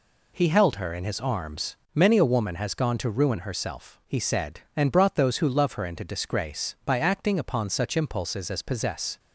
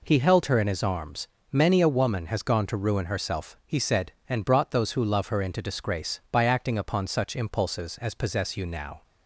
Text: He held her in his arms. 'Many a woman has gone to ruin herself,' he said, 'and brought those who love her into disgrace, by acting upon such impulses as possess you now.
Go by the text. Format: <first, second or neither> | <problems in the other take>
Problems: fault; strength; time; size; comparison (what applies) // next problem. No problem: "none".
second | stops before "you now"; at 9.1 s